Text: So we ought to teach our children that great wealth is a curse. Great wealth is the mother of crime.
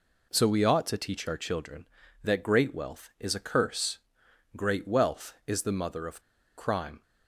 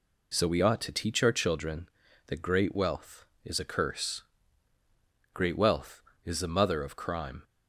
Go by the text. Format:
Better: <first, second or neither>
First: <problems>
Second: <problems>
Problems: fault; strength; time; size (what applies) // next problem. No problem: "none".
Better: second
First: pauses between "of" and "crime"; at 6.2 s; 0.36 s long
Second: none